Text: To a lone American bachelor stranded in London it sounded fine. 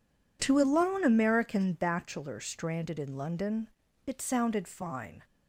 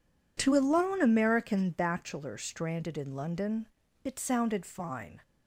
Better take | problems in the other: neither | pauses between "London" and "it"; slight; the same in both

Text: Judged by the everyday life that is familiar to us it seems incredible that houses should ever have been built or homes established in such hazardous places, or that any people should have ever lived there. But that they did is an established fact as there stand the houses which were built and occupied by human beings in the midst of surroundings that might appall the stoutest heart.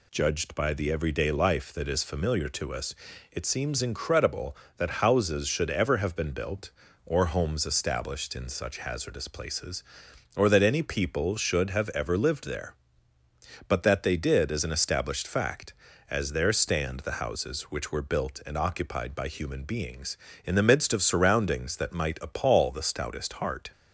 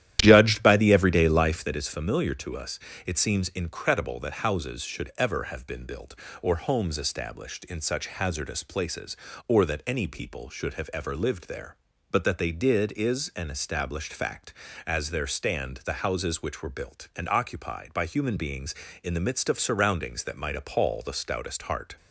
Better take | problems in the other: first | starts louder than the rest; strong; until 1.7 s; 12 dB // pauses between "us" and "it"; slight; at 2.7 s; 0.28 s long; slight in the first

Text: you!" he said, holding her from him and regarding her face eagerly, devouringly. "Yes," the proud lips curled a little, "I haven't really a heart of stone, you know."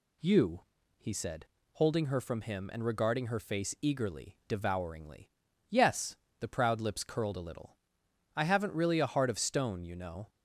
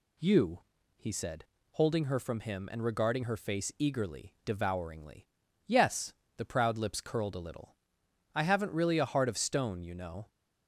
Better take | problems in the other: neither | none

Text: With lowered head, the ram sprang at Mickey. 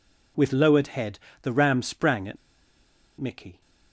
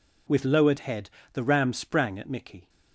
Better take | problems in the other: second | pauses between "at" and "Mickey"; noticeable; at 2.3 s; 0.81 s long

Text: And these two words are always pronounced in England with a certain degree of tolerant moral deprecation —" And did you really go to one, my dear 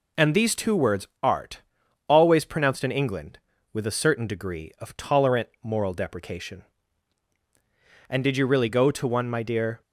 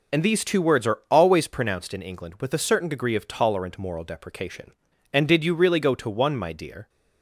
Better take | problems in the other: second | says "art" for "are"; at 1.2 s

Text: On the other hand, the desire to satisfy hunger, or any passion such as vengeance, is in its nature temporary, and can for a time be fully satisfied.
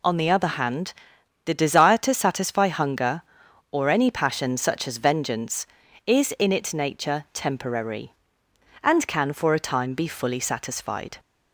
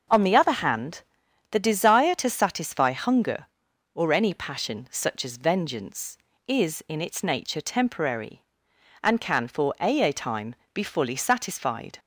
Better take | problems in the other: first | starts louder than the rest; noticeable; until 1.5 s; 6 dB // says "a" twice; at 10.0 s // pauses between "time" and "be"; slight; at 10.5 s; 0.18 s long

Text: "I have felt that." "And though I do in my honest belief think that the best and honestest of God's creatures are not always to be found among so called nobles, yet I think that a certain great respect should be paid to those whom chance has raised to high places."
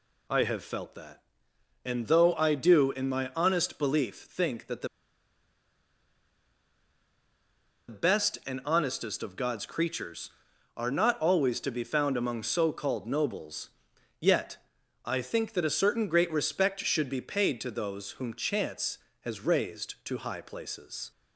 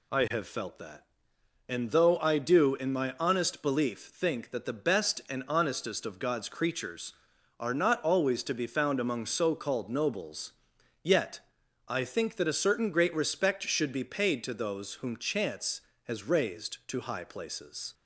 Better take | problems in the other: second | pauses between "the" and "best"; strong; at 4.8 s; 3.0 s long // pauses between "yet" and "I"; noticeable; at 14.5 s; 0.48 s long; noticeable in the second

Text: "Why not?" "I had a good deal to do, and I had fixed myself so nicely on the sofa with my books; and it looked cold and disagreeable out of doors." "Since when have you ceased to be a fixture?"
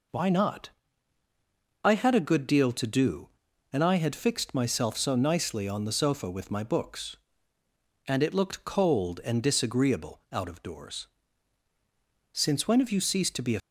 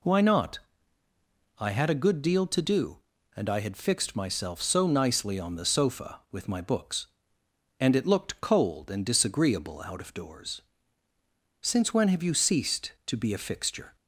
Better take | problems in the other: second | stops before "fixture"; at 13.5 s

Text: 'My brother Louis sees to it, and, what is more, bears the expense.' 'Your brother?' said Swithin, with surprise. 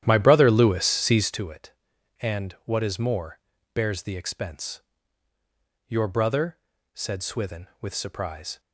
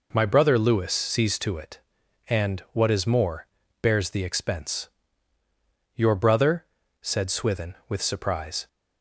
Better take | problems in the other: second | starts louder than the rest; strong; until 1.4 s; 11 dB

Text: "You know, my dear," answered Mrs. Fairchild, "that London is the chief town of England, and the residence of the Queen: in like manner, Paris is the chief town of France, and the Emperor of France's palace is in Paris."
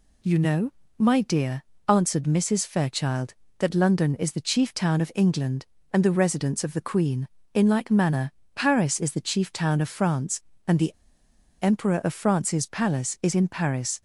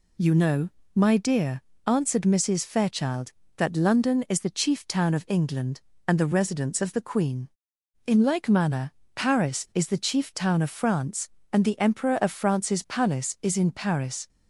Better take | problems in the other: second | pauses between "the" and "Emperor"; noticeable; at 10.9 s; 0.67 s long

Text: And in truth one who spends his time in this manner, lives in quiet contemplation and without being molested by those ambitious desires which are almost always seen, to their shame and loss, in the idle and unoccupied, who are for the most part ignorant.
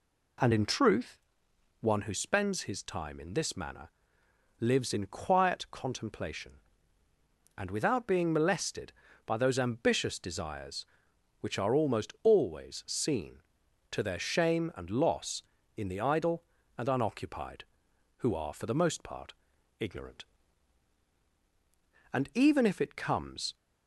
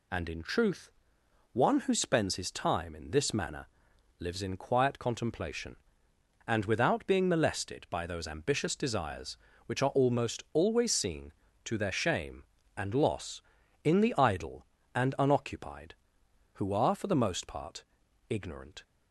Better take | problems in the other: second | pauses between "truth" and "one"; noticeable; at 1.1 s; 0.62 s long; noticeable in the second // pauses between "part" and "ignorant"; at 19.3 s; 0.44 s long; noticeable in the second // goes on to say "And even if it comes"; from 22.1 s on; 1.4 s long

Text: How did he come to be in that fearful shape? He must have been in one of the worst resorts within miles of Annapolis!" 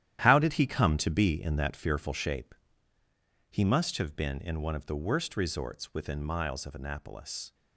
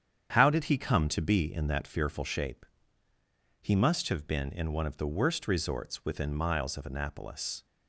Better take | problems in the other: second | gets quieter; strong; throughout; 11 dB // starts louder than the rest; strong; until 1.2 s; 11.5 dB; strong in the second

